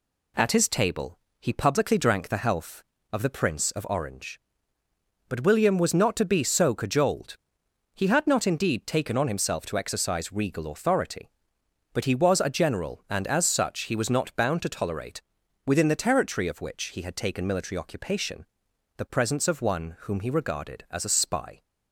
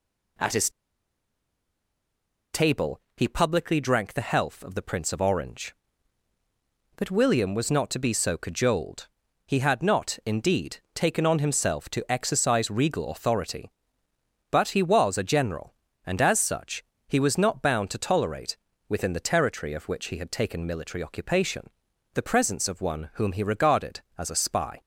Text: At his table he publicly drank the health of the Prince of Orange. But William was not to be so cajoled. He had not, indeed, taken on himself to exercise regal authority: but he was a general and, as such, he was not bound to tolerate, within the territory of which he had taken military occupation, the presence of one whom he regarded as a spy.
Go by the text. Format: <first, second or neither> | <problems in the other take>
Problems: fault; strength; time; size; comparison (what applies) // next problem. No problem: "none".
first | pauses between "his" and "table"; strong; at 0.7 s; 1.8 s long // pauses between "table" and "he"; slight; at 2.9 s; 0.16 s long; slight in the first